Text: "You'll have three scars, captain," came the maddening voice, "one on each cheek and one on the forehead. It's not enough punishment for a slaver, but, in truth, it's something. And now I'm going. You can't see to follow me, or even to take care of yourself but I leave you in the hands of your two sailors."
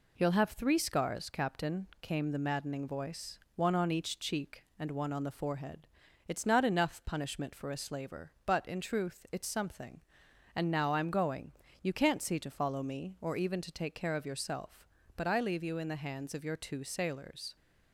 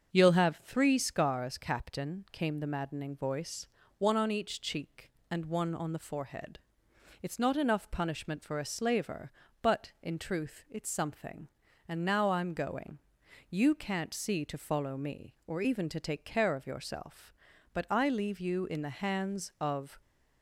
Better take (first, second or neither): first